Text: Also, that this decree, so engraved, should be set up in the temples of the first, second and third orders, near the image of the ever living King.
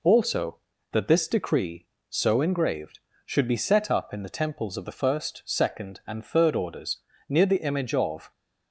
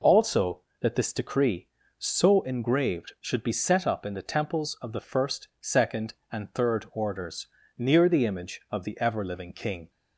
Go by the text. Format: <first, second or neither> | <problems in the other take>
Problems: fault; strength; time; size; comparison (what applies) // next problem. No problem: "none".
second | stops before "the ever living King"; at 8.3 s